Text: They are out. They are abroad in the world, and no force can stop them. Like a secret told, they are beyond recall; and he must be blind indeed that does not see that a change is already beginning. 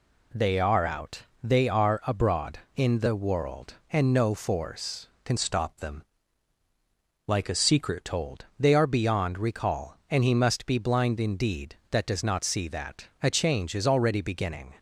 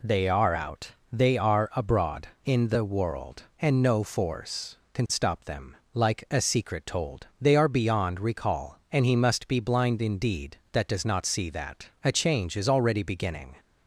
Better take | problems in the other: second | changes voice from "stop" to "secret"; from 5.3 to 8.0 s; 2.7 s long

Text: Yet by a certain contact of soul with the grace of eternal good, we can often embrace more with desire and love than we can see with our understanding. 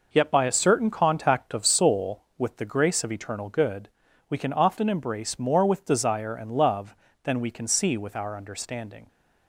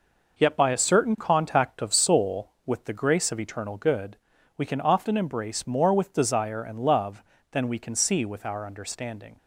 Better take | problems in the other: neither | none

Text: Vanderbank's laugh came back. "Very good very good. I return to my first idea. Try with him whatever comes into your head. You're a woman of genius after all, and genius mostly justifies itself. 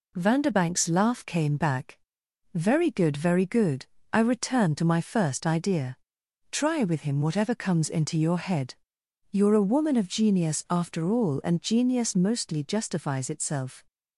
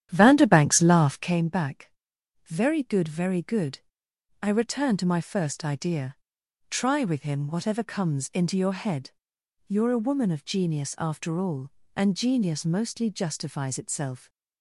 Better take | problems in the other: first | starts louder than the rest; strong; until 1.4 s; 10.5 dB

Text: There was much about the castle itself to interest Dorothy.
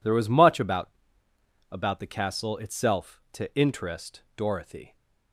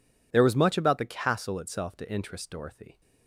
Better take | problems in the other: second | says "about" twice; at 1.7 s

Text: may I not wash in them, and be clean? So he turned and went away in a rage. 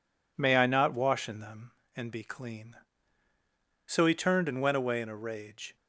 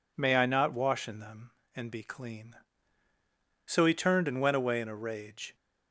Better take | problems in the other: second | gets quieter; noticeable; throughout; 4.5 dB

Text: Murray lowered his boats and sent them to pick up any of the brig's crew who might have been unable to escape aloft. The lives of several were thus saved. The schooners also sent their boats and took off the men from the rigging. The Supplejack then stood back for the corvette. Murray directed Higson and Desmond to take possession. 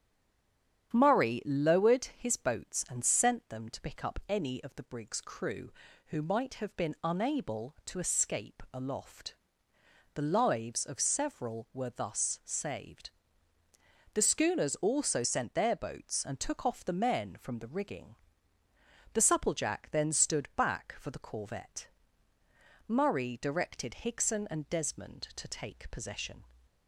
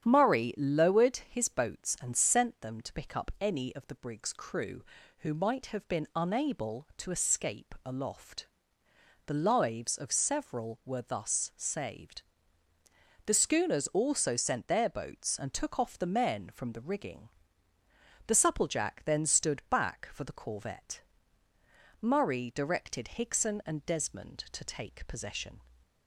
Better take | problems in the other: second | stays silent before the first word; slight; until 0.9 s; 0.9 s long // starts louder than the rest; strong; until 1.9 s; 9 dB; strong in the second

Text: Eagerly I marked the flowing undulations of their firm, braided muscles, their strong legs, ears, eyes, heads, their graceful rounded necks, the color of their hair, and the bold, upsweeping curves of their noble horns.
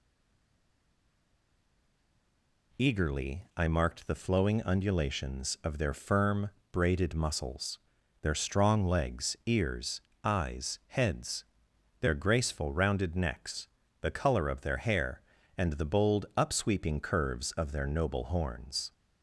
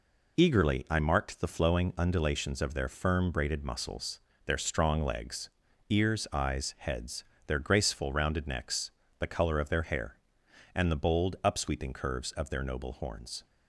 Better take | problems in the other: second | stays silent before the first word; strong; until 2.7 s; 2.7 s long

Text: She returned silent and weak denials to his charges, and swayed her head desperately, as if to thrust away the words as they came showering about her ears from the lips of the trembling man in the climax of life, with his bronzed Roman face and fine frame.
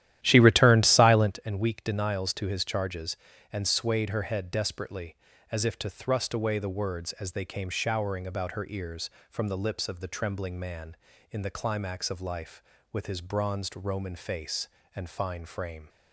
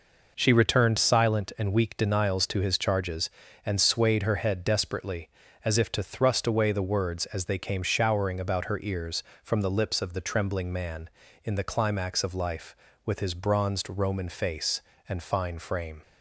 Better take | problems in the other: second | starts louder than the rest; strong; until 1.4 s; 12.5 dB

